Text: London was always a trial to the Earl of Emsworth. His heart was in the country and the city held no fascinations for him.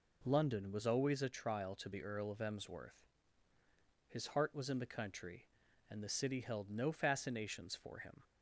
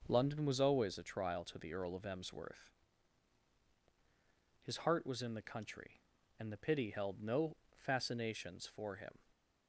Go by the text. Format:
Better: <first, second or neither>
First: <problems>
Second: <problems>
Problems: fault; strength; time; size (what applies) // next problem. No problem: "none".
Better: first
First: none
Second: starts louder than the rest; until 1.0 s; 6 dB // says "pity" for "city"; at 6.5 s // pauses between "no" and "fascinations"; slight; at 7.5 s; 0.22 s long